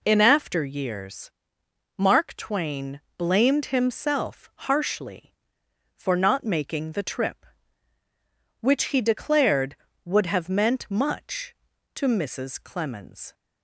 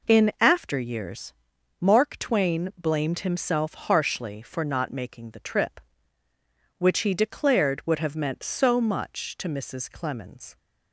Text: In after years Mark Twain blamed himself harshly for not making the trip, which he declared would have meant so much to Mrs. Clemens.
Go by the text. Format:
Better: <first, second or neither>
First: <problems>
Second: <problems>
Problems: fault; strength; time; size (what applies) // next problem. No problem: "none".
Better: second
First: pauses between "years" and "Mark"; noticeable; at 1.2 s; 0.66 s long // pauses between "Twain" and "blamed"; slight; at 3.0 s; 0.16 s long // pauses between "himself" and "harshly"; slight; at 4.4 s; 0.16 s long // skips "so"; at 10.8 s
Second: pauses between "years" and "Mark"; noticeable; at 1.3 s; 0.48 s long